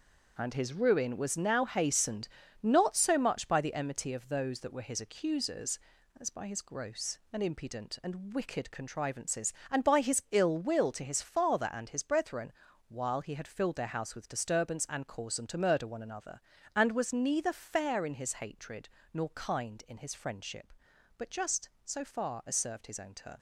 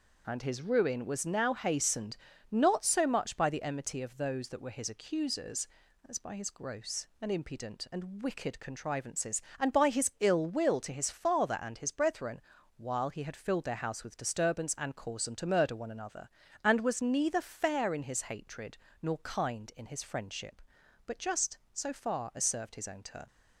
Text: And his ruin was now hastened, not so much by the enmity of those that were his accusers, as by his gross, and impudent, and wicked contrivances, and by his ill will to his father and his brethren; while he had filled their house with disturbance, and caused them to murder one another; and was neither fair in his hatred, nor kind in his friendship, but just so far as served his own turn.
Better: second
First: gets quieter; strong; throughout; 8 dB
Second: none

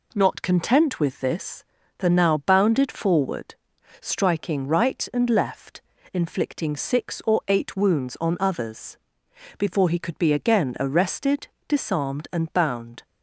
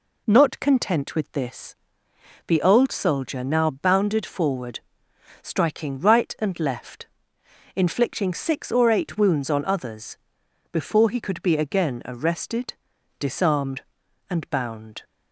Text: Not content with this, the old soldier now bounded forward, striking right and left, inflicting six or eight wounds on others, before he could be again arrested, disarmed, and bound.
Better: second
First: skips "old soldier"; at 2.0 s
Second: none

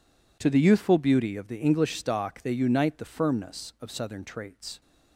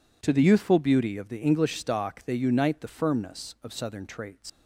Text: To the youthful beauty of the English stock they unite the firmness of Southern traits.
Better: first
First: none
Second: leaves "traits" unfinished; at 4.4 s; 125 ms

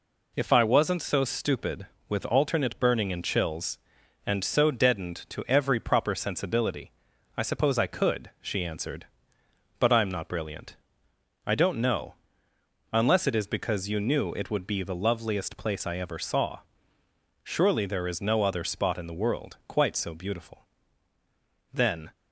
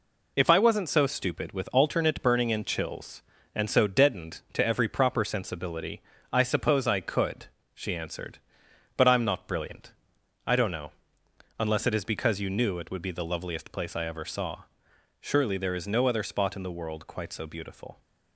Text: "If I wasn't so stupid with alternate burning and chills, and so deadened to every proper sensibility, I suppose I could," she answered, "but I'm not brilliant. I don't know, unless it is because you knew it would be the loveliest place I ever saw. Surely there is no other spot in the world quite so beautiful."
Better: second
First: goes on to say "Then"; slight; from 21.7 s on; 0.38 s long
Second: none

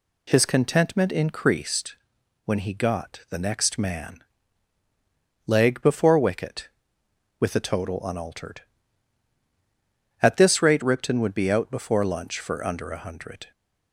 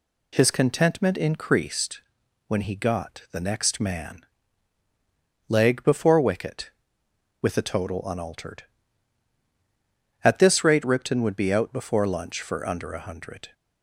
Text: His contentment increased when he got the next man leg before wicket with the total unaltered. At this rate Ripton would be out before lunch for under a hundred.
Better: neither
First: pauses between "increased" and "when"; noticeable; at 1.9 s; 0.50 s long // pauses between "man" and "leg"; at 4.2 s; 1.2 s long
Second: pauses between "increased" and "when"; noticeable; at 1.9 s; 0.48 s long // pauses between "man" and "leg"; at 4.2 s; 1.2 s long

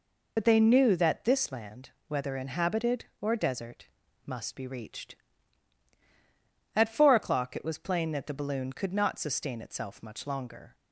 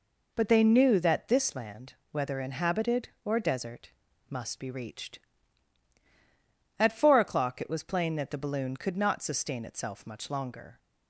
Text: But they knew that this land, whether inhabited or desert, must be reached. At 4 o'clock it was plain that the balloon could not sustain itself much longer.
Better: second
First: loses the start of "But"; at 0.3 s; 60 ms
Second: none

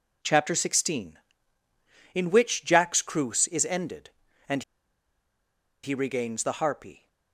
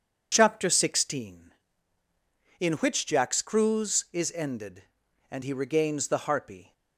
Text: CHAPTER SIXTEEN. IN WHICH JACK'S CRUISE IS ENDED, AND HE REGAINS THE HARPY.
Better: second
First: pauses between "AND" and "HE"; at 4.6 s; 1.2 s long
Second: none

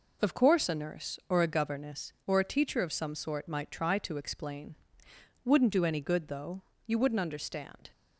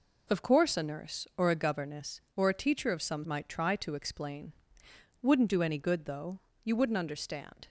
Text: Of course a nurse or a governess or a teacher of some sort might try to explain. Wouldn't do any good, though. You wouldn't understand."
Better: first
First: none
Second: skips "sort"; at 3.2 s

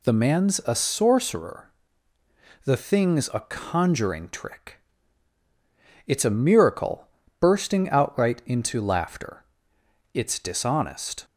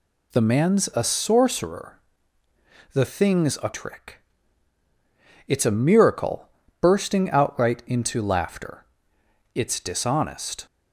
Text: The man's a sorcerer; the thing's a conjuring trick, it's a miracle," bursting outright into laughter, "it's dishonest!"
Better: first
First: none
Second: skips "conjuring"; at 3.7 s

